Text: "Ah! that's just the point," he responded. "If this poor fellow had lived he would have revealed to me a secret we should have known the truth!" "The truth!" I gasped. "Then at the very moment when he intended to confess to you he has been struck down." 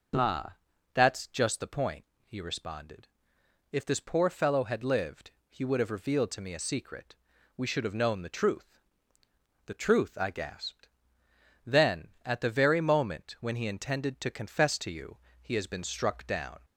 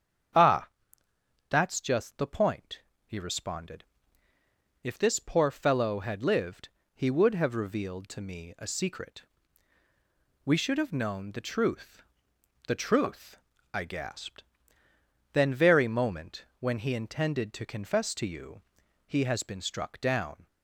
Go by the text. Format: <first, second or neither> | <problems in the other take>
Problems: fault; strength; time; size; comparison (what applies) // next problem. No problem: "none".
first | starts louder than the rest; strong; until 2.1 s; 8 dB // pauses between "lived" and "he"; slight; at 6.6 s; 0.26 s long; slight in the first // pauses between "secret" and "we"; at 9.2 s; 1.1 s long; also in the first // skips "at the"; at 15.5 s // pauses between "moment" and "when"; slight; at 16.4 s; 0.16 s long // pauses between "you" and "he"; at 18.6 s; 0.42 s long; slight in the first